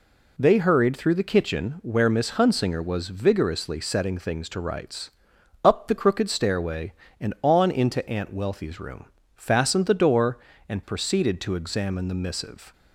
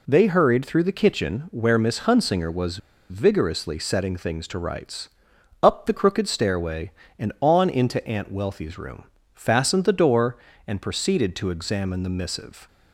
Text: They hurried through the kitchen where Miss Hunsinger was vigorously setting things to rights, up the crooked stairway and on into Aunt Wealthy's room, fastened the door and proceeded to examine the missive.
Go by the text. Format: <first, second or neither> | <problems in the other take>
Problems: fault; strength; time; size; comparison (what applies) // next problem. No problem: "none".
first | pauses between "was" and "vigorously"; slight; at 2.7 s; 0.32 s long